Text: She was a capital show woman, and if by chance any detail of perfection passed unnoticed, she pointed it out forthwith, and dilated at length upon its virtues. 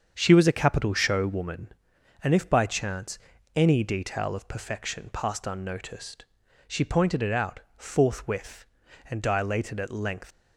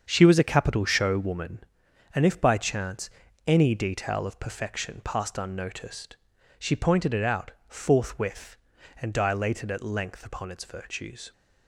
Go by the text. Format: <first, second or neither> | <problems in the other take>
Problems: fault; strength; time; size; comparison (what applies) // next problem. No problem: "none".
second | starts louder than the rest; strong; until 1.1 s; 7 dB; strong in the second // pauses between "chance" and "any"; at 3.1 s; 0.38 s long; also in the second // pauses between "out" and "forthwith"; slight; at 7.5 s; 0.18 s long; slight in the second // stops before "upon its virtues"; at 10.3 s